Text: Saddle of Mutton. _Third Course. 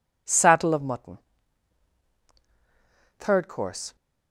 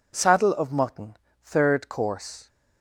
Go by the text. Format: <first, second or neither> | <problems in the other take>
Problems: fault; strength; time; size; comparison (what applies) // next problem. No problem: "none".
neither | none